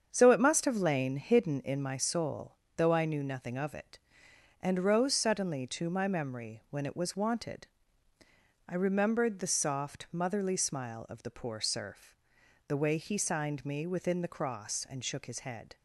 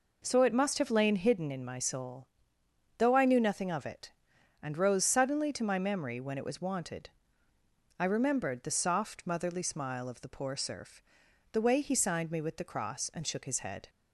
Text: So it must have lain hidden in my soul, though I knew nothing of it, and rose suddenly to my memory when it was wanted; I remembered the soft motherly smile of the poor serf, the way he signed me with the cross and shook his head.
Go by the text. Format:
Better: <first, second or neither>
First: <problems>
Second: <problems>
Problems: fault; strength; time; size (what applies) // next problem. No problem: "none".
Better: second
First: starts louder than the rest; strong; until 1.1 s; 7.5 dB // says "within" for "with"; at 13.8 s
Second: none